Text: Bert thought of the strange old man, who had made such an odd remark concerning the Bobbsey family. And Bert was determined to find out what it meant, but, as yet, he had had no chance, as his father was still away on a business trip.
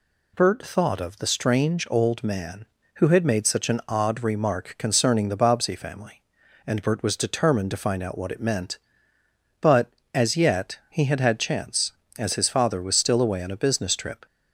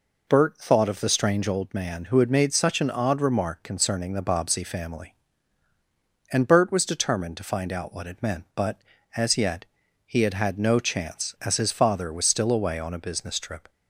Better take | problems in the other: second | skips "no"; at 11.3 s

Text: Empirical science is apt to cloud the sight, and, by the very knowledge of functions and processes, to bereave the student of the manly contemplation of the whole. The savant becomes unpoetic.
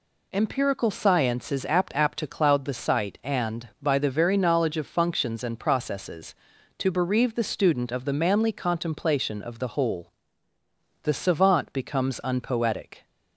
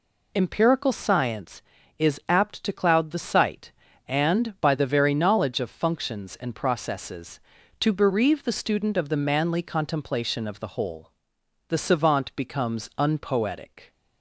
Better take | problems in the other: second | says "apt" twice; at 1.9 s

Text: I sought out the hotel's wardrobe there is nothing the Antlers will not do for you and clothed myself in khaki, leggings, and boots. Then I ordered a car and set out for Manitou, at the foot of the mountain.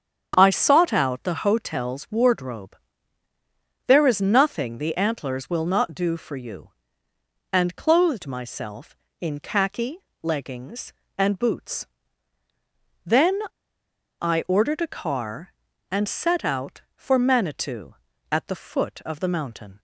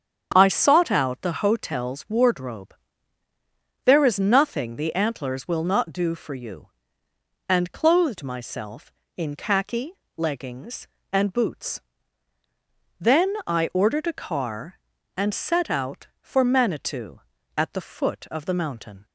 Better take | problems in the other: second | starts louder than the rest; strong; until 1.3 s; 8 dB; strong in the second // pauses between "wardrobe" and "there"; at 2.7 s; 1.1 s long; also in the second // pauses between "Then" and "I"; noticeable; at 13.3 s; 0.82 s long

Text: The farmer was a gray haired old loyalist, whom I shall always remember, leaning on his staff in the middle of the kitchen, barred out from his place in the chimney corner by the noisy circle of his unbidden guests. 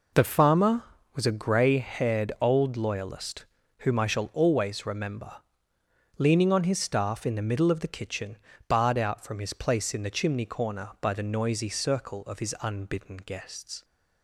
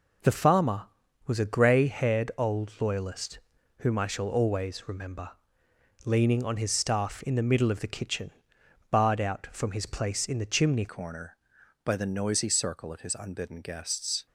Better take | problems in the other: first | changes voice at "corner"; from 10.8 s on; 3.4 s long

